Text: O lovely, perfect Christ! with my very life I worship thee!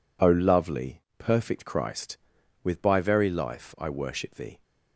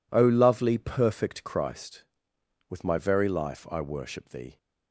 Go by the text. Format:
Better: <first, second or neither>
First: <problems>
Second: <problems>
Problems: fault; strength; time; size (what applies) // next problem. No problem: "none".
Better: second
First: says "by" for "my"; at 2.8 s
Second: none